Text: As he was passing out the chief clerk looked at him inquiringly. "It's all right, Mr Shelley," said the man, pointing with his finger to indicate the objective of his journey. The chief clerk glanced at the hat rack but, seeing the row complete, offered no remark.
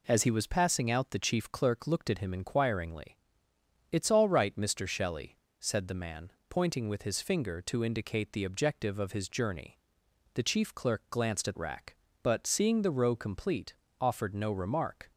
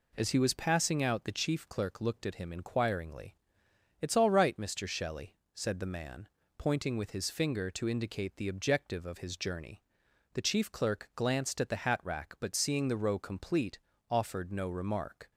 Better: second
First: skips "the hat"; at 11.5 s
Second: none

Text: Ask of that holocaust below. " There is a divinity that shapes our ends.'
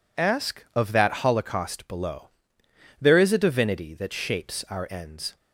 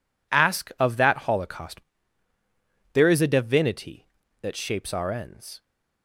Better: first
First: none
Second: skips "below"; at 2.0 s

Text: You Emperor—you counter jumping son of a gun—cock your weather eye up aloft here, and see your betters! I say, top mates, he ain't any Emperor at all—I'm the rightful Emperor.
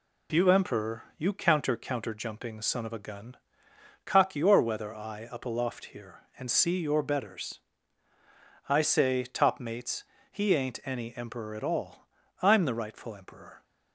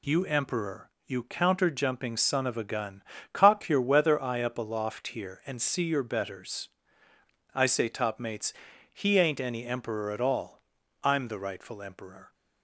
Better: second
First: says "counter" twice; at 1.7 s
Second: none

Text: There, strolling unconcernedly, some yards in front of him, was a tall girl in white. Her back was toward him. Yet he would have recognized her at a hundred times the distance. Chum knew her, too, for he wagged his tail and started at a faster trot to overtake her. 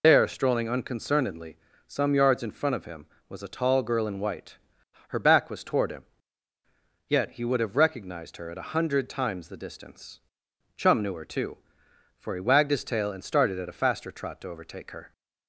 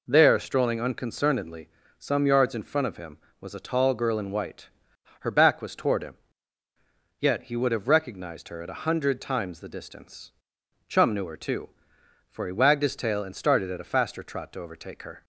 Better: second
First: loses the start of "There"; at 0.0 s; 85 ms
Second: none

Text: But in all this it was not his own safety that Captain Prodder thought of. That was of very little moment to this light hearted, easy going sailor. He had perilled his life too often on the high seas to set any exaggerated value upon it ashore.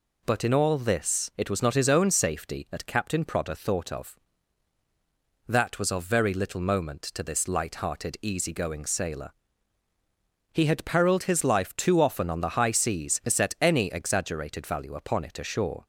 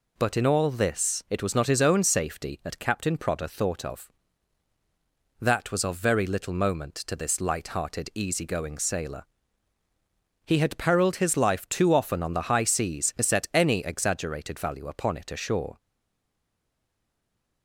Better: first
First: none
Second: stays silent after the last word; noticeable; from 15.7 s on; 1.9 s long

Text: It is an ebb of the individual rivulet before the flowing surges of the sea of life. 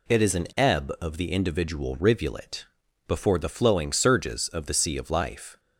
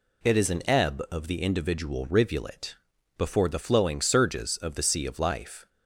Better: neither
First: pauses between "rivulet" and "before"; at 2.6 s; 0.42 s long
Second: pauses between "rivulet" and "before"; at 2.7 s; 0.42 s long

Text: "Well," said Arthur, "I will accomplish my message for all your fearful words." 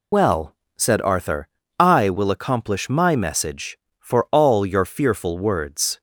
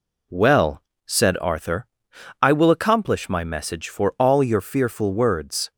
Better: second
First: loses the start of "Well"; at 0.1 s; 115 ms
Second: none

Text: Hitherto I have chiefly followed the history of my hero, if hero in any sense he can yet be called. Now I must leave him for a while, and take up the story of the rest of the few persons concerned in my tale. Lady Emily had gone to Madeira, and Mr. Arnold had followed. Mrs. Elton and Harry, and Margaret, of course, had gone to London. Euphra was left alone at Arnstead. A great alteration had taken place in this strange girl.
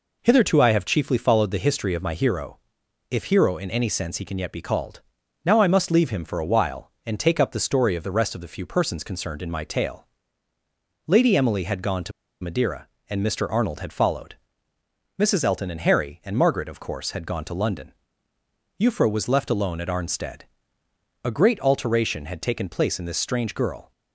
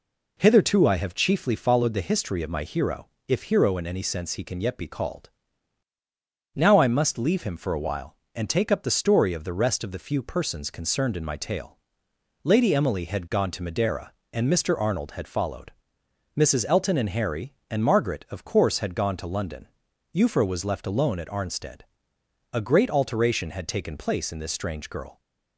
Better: second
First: pauses between "to" and "Madeira"; slight; at 12.1 s; 0.31 s long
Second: none

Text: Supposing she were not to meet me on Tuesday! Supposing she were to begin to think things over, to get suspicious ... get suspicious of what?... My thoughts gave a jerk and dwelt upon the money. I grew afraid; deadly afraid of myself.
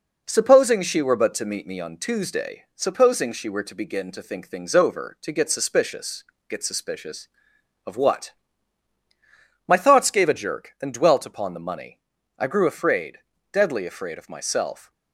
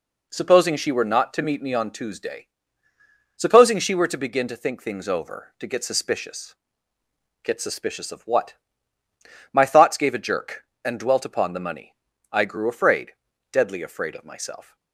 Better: second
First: says "but" for "not"; at 1.1 s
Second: none

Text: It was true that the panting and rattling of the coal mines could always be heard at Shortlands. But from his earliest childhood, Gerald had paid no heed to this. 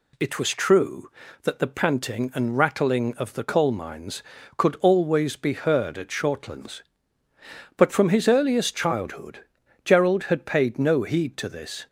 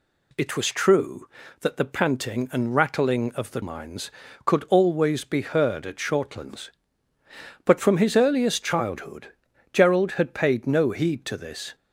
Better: first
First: none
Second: skips "coal"; at 3.6 s

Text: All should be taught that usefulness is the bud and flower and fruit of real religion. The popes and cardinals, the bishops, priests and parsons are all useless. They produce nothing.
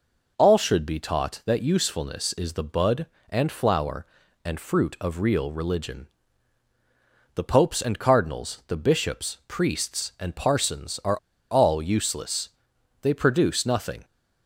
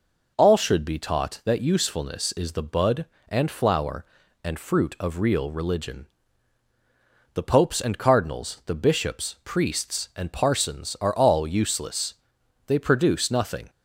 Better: second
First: pauses between "are" and "all"; slight; at 11.1 s; 0.31 s long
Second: none

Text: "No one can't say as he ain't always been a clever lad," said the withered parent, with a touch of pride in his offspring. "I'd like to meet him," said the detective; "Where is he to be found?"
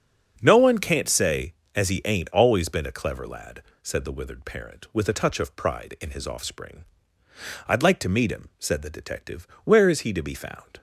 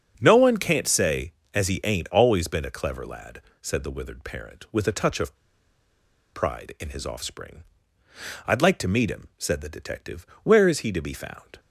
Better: first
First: starts louder than the rest; until 1.4 s; 7 dB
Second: starts louder than the rest; until 1.2 s; 7 dB // pauses between "of" and "pride"; noticeable; at 5.3 s; 0.98 s long

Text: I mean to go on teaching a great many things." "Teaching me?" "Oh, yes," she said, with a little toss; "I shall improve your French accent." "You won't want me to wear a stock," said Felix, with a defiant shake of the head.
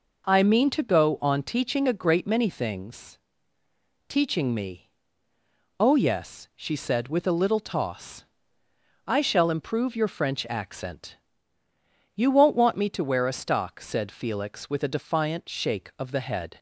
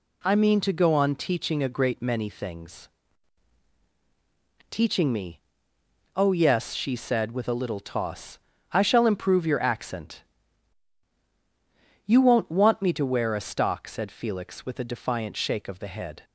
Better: first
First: none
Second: skips "French"; at 9.6 s

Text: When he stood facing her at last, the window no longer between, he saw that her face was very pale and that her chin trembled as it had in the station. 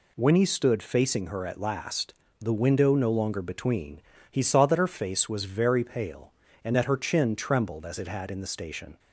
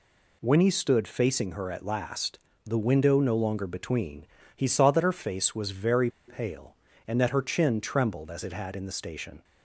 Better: first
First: none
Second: pauses between "very" and "pale"; slight; at 6.1 s; 0.17 s long

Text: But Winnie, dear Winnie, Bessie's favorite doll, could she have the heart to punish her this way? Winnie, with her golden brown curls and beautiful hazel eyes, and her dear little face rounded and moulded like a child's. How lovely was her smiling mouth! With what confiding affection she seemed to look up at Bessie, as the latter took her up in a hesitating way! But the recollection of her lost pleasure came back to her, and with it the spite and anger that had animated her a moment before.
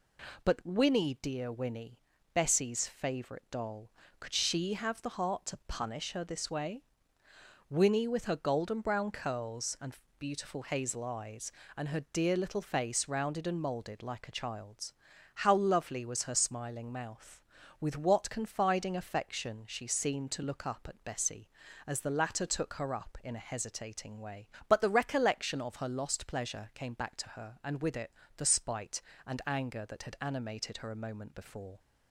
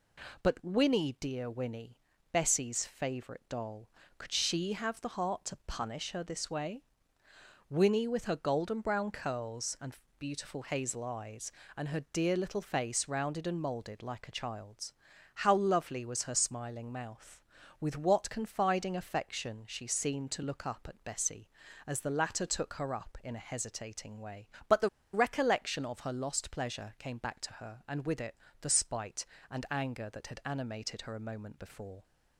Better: first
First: pauses between "and" and "beautiful"; slight; at 9.9 s; 0.22 s long // pauses between "it" and "the"; slight; at 28.1 s; 0.26 s long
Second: pauses between "and" and "beautiful"; slight; at 9.9 s; 0.22 s long // pauses between "the" and "recollection"; slight; at 24.8 s; 0.24 s long // pauses between "it" and "the"; slight; at 28.3 s; 0.26 s long

